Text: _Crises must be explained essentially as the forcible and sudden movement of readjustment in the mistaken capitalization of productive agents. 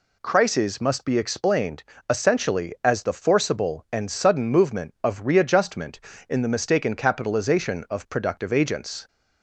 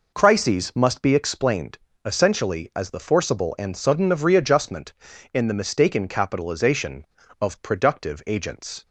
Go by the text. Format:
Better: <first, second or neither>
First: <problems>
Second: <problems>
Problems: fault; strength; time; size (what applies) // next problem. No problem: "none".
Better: first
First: pauses between "explained" and "essentially"; slight; at 1.8 s; 0.26 s long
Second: pauses between "explained" and "essentially"; slight; at 1.7 s; 0.26 s long // skips "movement"; at 4.1 s